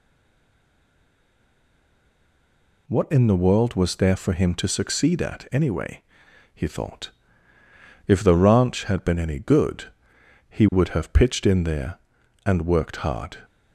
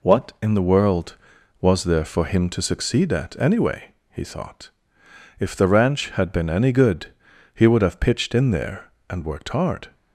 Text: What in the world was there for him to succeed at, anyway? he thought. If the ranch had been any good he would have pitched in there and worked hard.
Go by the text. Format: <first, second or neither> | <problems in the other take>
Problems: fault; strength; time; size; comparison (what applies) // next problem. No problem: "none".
second | stays silent before the first word; strong; until 2.8 s; 2.8 s long // pauses between "good" and "he"; noticeable; at 9.8 s; 0.64 s long; also in the second